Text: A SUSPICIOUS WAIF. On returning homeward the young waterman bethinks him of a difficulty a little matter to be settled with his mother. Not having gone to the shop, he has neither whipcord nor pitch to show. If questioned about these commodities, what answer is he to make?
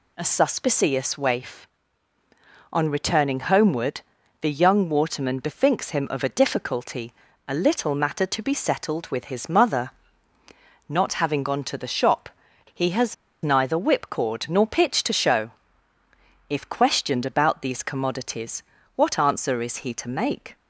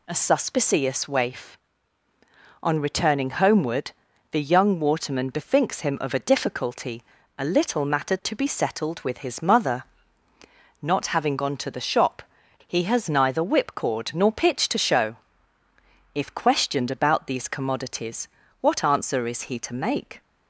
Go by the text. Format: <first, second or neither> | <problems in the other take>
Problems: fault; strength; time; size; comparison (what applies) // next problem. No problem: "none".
second | pauses between "homeward" and "the"; at 4.0 s; 0.40 s long; also in the second // pauses between "difficulty" and "a"; slight; at 7.1 s; 0.34 s long; slight in the second // pauses between "has" and "neither"; slight; at 13.1 s; 0.29 s long